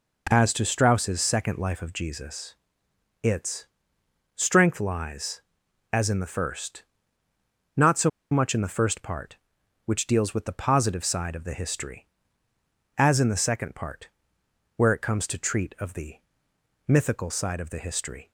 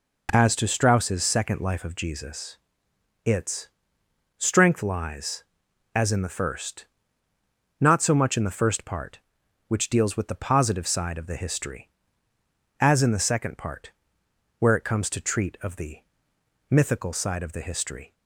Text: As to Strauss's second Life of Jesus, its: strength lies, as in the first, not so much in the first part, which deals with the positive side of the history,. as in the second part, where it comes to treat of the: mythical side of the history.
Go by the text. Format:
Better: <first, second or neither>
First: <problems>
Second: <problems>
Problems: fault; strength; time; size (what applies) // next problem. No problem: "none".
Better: second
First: pauses between "so" and "much"; slight; at 8.0 s; 0.21 s long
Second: none